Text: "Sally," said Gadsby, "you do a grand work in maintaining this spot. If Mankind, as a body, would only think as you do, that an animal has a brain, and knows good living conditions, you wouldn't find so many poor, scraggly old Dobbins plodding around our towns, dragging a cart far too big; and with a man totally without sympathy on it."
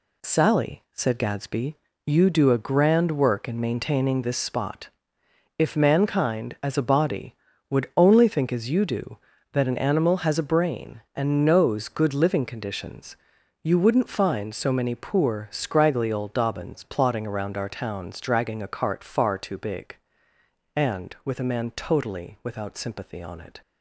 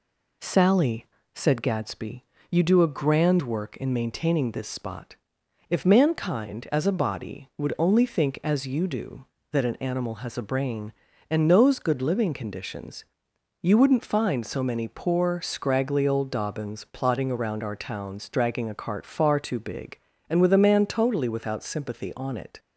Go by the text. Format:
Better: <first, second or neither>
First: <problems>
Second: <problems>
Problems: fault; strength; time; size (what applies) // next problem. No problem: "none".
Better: neither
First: none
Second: none